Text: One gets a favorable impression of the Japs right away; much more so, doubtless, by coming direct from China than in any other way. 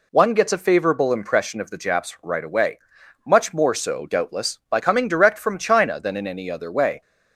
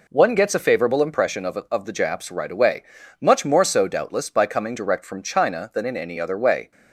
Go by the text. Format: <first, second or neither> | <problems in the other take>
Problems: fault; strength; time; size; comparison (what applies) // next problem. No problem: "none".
first | says "of" twice; at 1.7 s